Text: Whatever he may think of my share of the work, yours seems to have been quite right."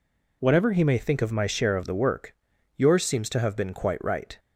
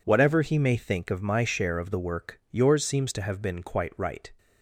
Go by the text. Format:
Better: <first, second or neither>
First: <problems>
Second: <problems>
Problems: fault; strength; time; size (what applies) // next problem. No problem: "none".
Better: neither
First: none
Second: none